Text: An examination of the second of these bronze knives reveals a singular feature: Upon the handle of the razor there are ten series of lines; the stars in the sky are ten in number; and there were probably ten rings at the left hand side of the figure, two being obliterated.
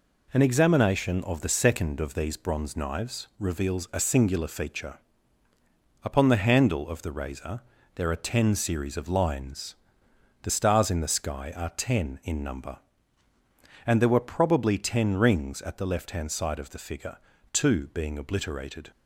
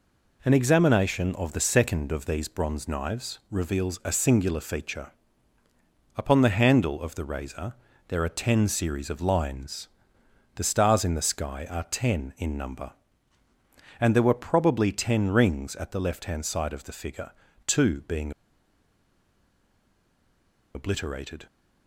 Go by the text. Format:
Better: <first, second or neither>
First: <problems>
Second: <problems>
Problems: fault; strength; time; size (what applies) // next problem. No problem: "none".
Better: first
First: pauses between "razor" and "there"; slight; at 7.6 s; 0.34 s long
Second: pauses between "razor" and "there"; slight; at 7.7 s; 0.34 s long // pauses between "being" and "obliterated"; strong; at 18.3 s; 2.4 s long